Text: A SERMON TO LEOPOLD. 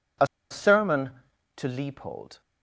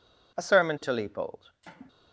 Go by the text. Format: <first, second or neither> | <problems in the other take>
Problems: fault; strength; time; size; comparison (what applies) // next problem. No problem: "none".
second | pauses between "A" and "SERMON"; slight; at 0.2 s; 0.23 s long